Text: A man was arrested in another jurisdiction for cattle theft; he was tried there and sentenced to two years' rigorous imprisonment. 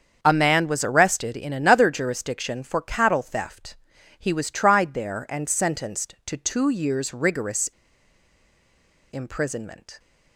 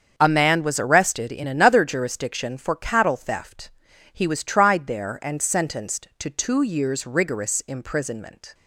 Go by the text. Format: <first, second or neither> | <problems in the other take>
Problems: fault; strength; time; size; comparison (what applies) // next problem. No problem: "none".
second | starts louder than the rest; strong; until 1.2 s; 7 dB; also in the second // pauses between "rigorous" and "imprisonment"; strong; at 7.6 s; 1.4 s long